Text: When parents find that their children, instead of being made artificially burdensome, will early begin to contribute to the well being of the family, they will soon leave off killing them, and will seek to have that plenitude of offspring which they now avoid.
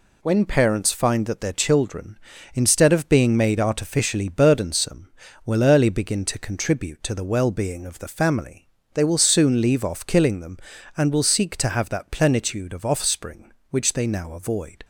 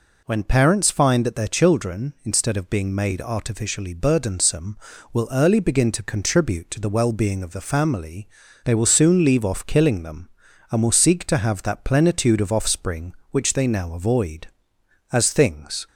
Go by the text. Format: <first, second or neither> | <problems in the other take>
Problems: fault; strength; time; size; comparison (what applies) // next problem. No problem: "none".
first | goes on to say "As things"; noticeable; from 15.1 s on; 0.76 s long